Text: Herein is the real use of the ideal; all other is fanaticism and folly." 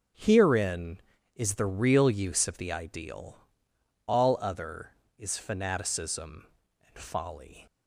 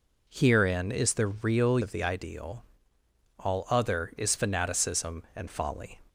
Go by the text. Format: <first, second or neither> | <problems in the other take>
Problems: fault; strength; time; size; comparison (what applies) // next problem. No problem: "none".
first | skips "use"; at 1.7 s